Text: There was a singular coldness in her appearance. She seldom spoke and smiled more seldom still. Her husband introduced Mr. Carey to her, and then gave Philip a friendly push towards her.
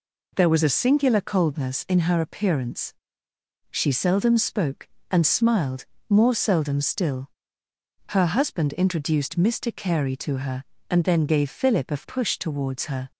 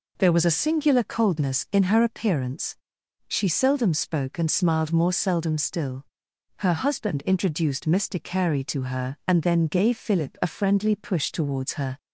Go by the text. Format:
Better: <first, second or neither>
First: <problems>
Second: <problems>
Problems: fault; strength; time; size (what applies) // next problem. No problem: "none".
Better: second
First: pauses between "smiled" and "more"; slight; at 5.8 s; 0.24 s long // skips "friendly"; at 12.0 s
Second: none